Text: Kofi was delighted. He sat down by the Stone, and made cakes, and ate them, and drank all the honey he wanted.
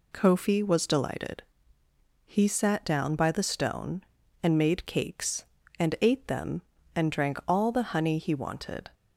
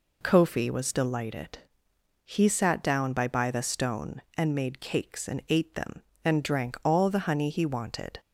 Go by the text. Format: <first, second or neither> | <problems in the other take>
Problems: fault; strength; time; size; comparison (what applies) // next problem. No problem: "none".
first | says "by" twice; at 3.2 s